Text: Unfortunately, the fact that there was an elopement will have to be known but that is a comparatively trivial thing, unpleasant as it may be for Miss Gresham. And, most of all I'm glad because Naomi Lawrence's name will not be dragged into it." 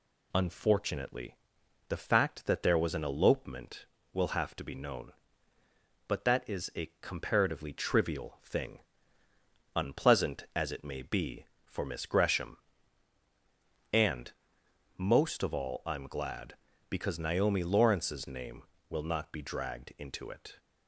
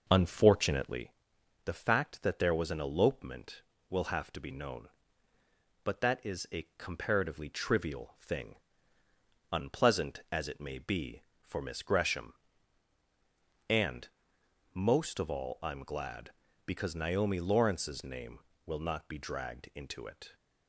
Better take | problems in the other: first | starts louder than the rest; noticeable; until 1.1 s; 5.5 dB

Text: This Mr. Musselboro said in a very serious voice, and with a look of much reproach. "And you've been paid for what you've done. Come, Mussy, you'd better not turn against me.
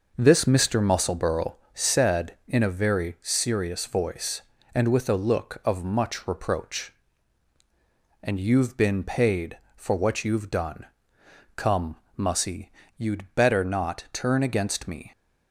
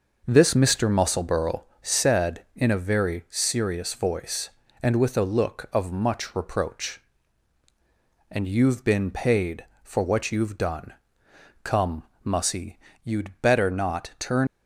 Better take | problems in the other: first | pauses between "Musselboro" and "said"; slight; at 1.6 s; 0.18 s long; slight in the first // stops before "against me"; at 14.4 s

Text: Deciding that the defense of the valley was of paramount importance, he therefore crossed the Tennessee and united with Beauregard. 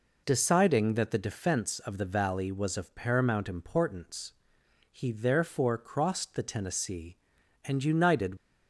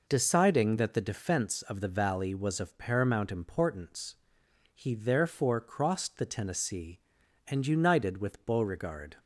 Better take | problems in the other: second | stops before "with Beauregard"; at 8.3 s

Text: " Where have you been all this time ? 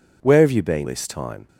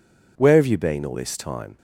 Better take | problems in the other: second | skips "all"; at 0.8 s

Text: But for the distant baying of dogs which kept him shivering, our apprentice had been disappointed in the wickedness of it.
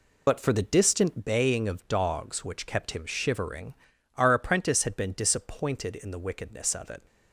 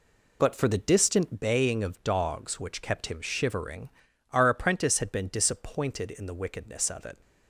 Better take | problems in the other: second | loses the start of "But"; at 0.2 s; 25 ms

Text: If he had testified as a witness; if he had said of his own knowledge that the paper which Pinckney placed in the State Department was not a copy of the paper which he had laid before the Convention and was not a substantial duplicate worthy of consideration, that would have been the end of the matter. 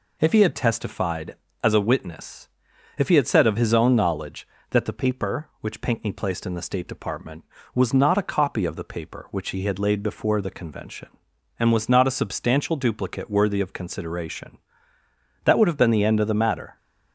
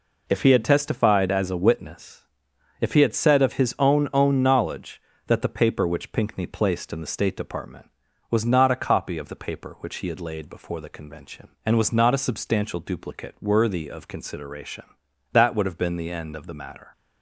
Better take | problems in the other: first | says "own" twice; at 4.1 s

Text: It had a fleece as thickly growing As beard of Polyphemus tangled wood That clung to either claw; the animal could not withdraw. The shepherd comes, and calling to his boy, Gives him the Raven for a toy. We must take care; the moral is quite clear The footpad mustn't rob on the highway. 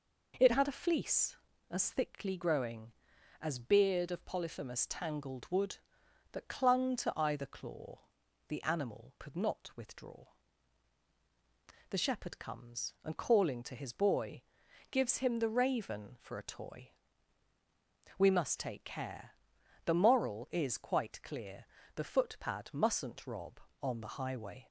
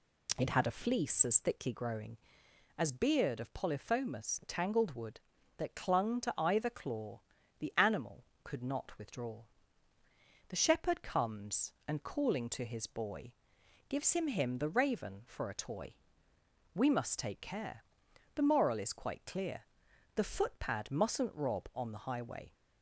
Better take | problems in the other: first | says "him" twice; at 14.2 s // pauses between "clear" and "The"; noticeable; at 19.6 s; 0.50 s long; slight in the first

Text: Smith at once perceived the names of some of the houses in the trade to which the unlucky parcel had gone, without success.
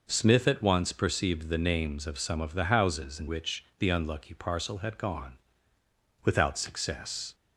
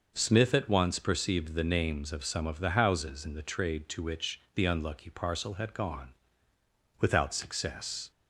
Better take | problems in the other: second | skips "the trade to"; at 3.2 s

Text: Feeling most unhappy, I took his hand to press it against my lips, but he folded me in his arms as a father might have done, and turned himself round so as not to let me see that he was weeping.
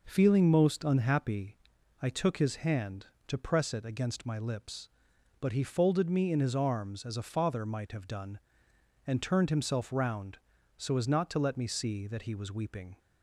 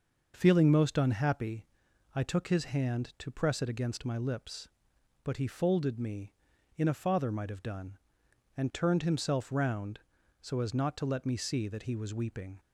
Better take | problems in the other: first | skips "his arms as"; at 6.8 s

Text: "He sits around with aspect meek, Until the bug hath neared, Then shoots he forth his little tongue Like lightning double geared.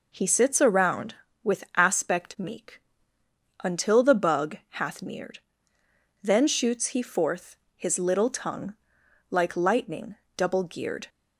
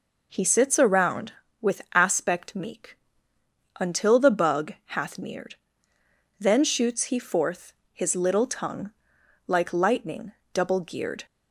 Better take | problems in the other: neither | pauses between "bug" and "hath"; slight; the same in both // pauses between "forth" and "his"; slight; the same in both // pauses between "tongue" and "Like"; noticeable; the same in both // pauses between "lightning" and "double"; slight; the same in both

